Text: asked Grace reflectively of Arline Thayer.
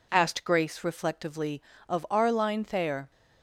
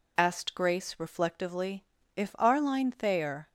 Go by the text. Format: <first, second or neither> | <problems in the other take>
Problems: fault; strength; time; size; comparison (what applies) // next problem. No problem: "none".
first | says "if" for "of"; at 2.1 s